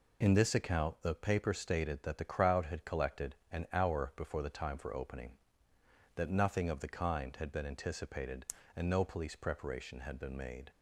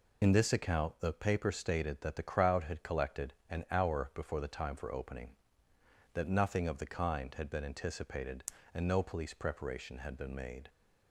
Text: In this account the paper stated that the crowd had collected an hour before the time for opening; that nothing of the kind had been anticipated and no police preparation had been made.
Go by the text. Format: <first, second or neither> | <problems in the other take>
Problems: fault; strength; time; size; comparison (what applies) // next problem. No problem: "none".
first | loses the start of "In"; at 0.2 s; 30 ms // pauses between "collected" and "an"; slight; at 3.3 s; 0.16 s long; slight in the first